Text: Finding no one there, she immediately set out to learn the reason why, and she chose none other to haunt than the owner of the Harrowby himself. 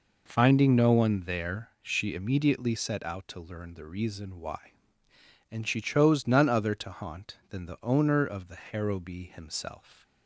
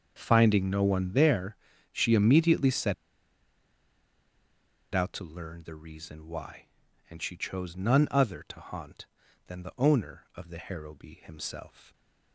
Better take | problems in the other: first | starts louder than the rest; until 1.1 s; 6.5 dB // pauses between "set" and "out"; strong; at 2.9 s; 2.0 s long

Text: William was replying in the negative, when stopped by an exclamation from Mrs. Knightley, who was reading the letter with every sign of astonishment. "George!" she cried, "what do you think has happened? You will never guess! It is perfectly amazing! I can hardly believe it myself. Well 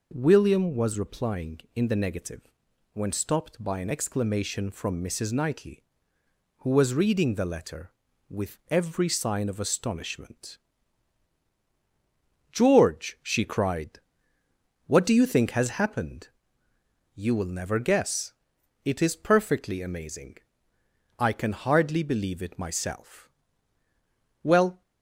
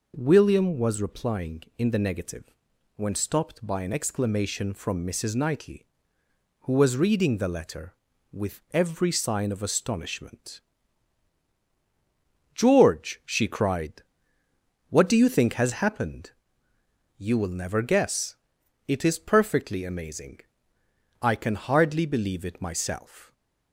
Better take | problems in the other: first | stops before "Well"; at 23.3 s

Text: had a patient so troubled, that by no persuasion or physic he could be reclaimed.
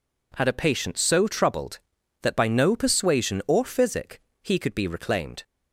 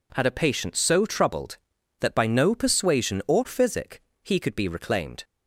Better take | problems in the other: neither | pauses between "physic" and "he"; slight; the same in both

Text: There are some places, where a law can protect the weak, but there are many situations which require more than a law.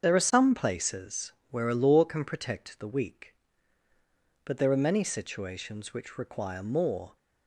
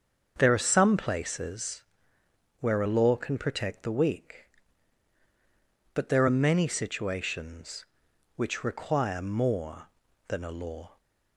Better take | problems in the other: second | starts louder than the rest; until 1.0 s; 7 dB; also in the second // stops before "than a law"; at 7.1 s

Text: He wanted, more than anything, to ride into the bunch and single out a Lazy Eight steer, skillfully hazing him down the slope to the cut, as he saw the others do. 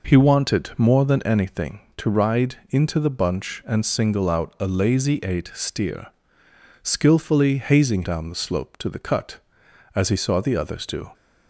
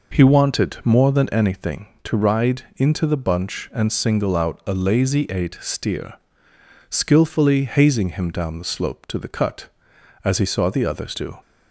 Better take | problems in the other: second | skips "him"; at 8.0 s

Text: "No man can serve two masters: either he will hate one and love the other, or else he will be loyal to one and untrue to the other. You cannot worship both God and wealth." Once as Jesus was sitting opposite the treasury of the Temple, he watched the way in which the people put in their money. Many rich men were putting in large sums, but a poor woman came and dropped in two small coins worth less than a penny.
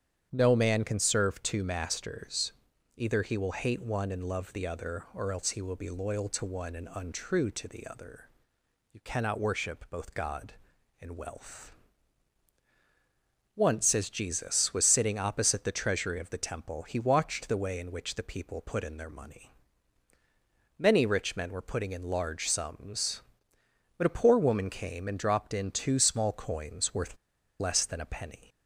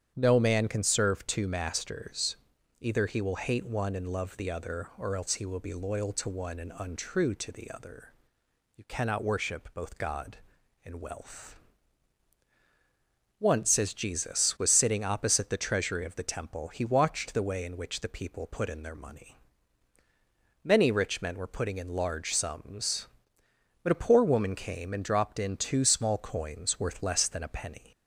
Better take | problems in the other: second | starts louder than the rest; strong; until 1.3 s; 9 dB; strong in the second // pauses between "worth" and "less"; at 27.1 s; 0.43 s long

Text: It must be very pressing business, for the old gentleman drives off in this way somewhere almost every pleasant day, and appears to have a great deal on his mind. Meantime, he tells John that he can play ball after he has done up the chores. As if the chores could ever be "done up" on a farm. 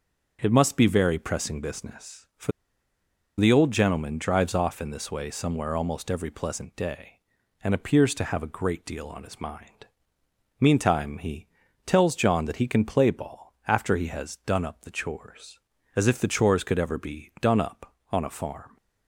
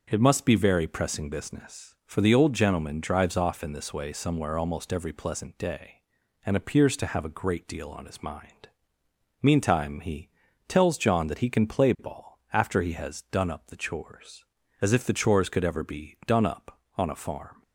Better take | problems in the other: second | starts louder than the rest; until 1.4 s; 6.5 dB; also in the second // pauses between "for" and "the"; noticeable; at 2.5 s; 0.89 s long // pauses between "he" and "tells"; at 11.4 s; 0.38 s long; also in the second

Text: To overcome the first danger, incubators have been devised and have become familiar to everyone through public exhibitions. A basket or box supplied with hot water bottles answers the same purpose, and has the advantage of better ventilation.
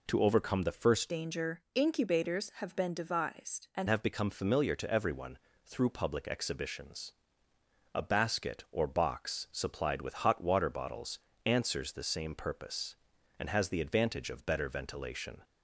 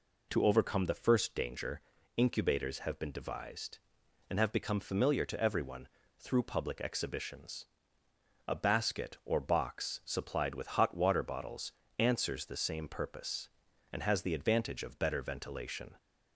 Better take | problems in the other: second | changes voice from "danger" to "and"; from 1.0 to 3.8 s; 2.8 s long // pauses between "everyone" and "through"; slight; at 5.3 s; 0.28 s long; slight in the second // pauses between "bottles" and "answers"; slight; at 11.1 s; 0.26 s long; slight in the second

